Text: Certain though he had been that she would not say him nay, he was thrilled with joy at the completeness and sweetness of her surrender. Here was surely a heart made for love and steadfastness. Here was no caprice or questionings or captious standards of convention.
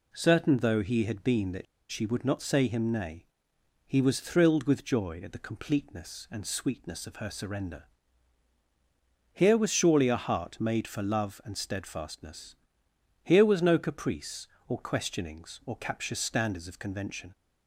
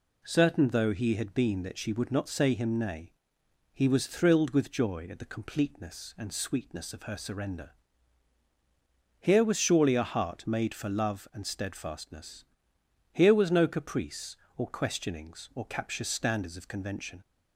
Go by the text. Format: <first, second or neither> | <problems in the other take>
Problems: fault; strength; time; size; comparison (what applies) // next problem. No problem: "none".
second | pauses between "that" and "she"; slight; at 1.6 s; 0.26 s long